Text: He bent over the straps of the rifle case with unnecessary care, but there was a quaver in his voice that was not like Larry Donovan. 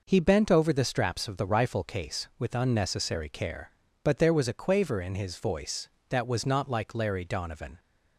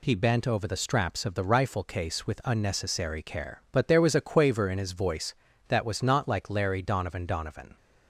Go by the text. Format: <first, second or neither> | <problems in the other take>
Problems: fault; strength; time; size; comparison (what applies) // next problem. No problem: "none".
first | says "Donovan" twice; at 7.2 s